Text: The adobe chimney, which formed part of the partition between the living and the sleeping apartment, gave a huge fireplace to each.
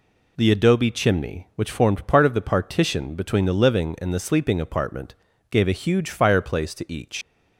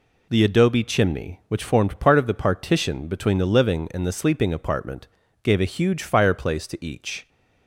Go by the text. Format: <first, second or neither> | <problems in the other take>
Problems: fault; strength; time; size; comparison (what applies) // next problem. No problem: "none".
second | leaves "each" unfinished; at 7.2 s; 140 ms